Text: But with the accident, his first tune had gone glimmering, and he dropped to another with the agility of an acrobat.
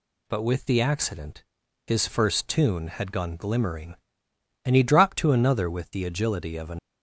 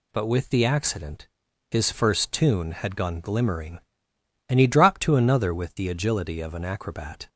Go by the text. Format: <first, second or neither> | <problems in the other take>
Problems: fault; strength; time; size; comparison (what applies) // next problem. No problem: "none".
second | stops before "acrobat"; at 6.7 s